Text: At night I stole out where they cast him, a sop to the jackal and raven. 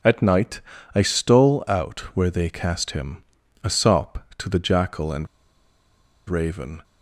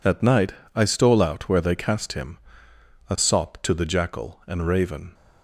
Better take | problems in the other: second | pauses between "night" and "I"; slight; at 0.6 s; 0.34 s long; slight in the second // pauses between "out" and "where"; slight; at 1.9 s; 0.16 s long // pauses between "and" and "raven"; at 5.2 s; 1.0 s long

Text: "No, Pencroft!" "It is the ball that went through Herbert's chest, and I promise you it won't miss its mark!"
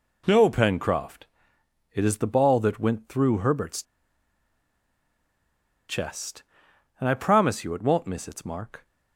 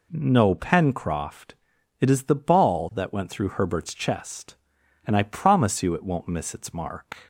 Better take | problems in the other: second | pauses between "Herbert's" and "chest"; strong; at 3.8 s; 2.0 s long

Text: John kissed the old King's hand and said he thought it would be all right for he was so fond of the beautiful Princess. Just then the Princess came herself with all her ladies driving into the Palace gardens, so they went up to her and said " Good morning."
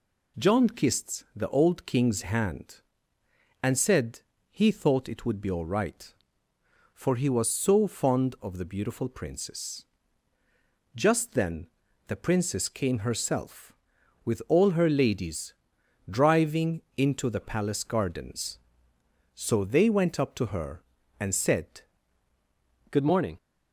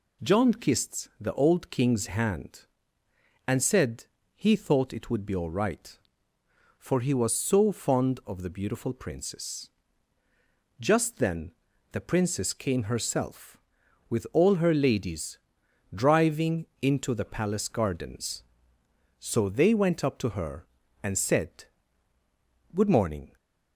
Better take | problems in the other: second | pauses between "said" and "he"; slight; at 4.2 s; 0.30 s long; slight in the second // pauses between "then" and "the"; at 11.6 s; 0.40 s long; also in the second // pauses between "ladies" and "driving"; noticeable; at 15.5 s; 0.56 s long; noticeable in the second // pauses between "driving" and "into"; slight; at 16.8 s; 0.16 s long; slight in the second // changes voice at "Good"; from 22.9 s on; 0.4 s long

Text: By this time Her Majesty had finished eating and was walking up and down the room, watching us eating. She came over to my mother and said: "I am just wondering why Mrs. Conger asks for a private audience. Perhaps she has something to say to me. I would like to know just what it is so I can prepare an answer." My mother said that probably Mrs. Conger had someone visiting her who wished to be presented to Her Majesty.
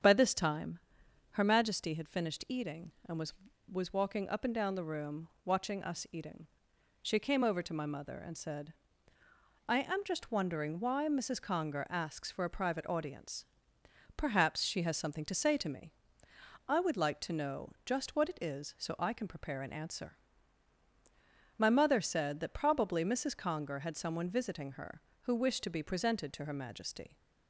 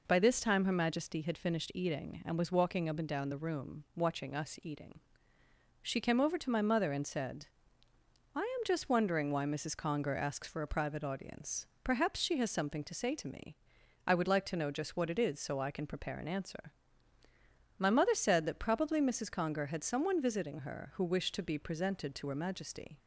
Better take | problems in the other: second | starts louder than the rest; strong; until 1.5 s; 7.5 dB // pauses between "time" and "Her"; noticeable; at 0.8 s; 0.50 s long // says "was" twice; at 3.7 s

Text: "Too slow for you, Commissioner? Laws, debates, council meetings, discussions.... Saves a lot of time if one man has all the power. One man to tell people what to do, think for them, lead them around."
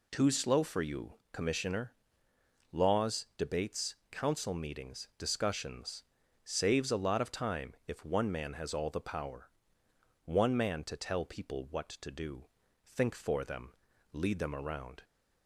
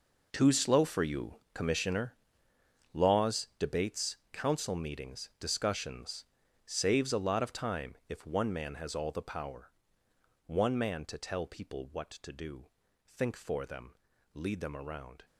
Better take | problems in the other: first | gets quieter; strong; throughout; 13.5 dB

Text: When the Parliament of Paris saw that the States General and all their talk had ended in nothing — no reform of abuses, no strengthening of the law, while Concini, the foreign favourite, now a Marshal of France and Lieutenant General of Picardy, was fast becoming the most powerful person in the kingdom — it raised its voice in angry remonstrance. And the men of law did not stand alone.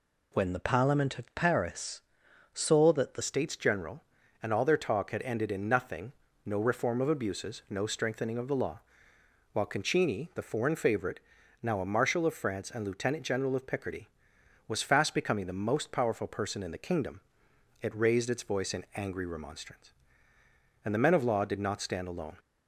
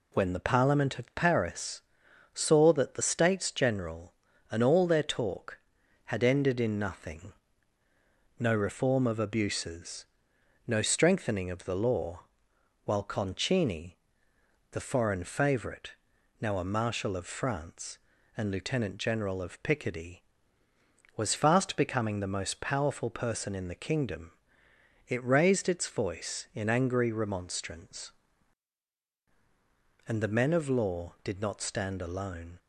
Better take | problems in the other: second | pauses between "Paris" and "saw"; noticeable; at 2.0 s; 0.54 s long; noticeable in the second // changes voice at "States"; from 3.2 s on; 19.1 s long

